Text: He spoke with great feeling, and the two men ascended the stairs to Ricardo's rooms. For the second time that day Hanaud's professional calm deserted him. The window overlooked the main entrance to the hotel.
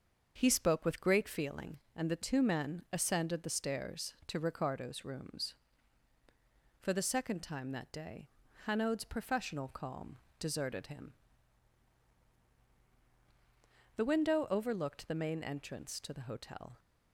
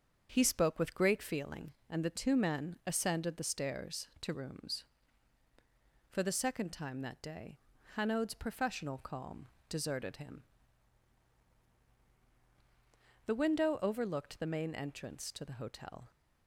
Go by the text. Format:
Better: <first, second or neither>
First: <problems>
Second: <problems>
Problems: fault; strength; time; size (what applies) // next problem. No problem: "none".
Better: first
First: starts louder than the rest; until 1.3 s; 6.5 dB // pauses between "day" and "Hanaud's"; at 8.2 s; 0.38 s long // pauses between "calm" and "deserted"; slight; at 10.1 s; 0.20 s long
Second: starts louder than the rest; until 1.3 s; 7 dB // skips "Ricardo's"; at 4.3 s // pauses between "day" and "Hanaud's"; at 7.5 s; 0.38 s long // pauses between "calm" and "deserted"; slight; at 9.4 s; 0.20 s long